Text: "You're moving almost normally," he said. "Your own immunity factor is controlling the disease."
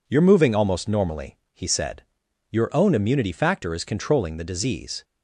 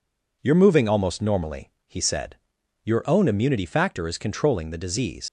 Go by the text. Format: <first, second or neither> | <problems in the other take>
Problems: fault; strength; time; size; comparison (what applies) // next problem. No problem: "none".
first | leaves "disease" unfinished; at 5.2 s; 85 ms